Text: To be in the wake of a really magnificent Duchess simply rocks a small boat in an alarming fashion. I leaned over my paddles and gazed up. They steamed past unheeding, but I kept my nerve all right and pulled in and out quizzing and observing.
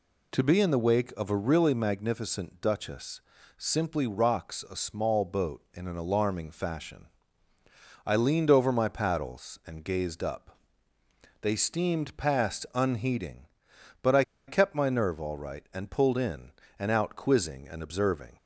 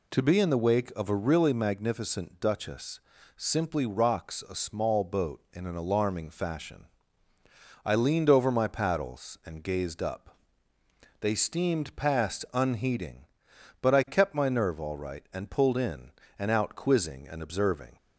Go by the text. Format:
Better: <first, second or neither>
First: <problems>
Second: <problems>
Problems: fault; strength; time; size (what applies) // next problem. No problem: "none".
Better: second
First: pauses between "Duchess" and "simply"; at 3.1 s; 0.38 s long // pauses between "I" and "kept"; slight; at 14.2 s; 0.25 s long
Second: pauses between "Duchess" and "simply"; at 2.9 s; 0.38 s long